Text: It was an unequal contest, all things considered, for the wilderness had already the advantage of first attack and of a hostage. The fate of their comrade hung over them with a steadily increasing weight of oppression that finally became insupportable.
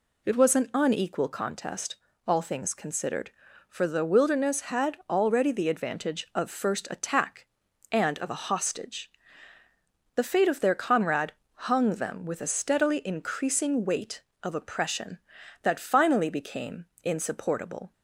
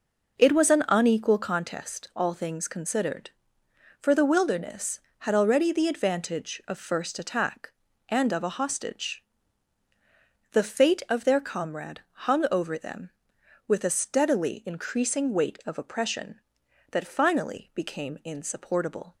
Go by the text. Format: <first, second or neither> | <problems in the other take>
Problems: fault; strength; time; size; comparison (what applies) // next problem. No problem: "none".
second | pauses between "comrade" and "hung"; slight; at 11.3 s; 0.22 s long // skips "over"; at 11.9 s // pauses between "became" and "insupportable"; slight; at 16.8 s; 0.18 s long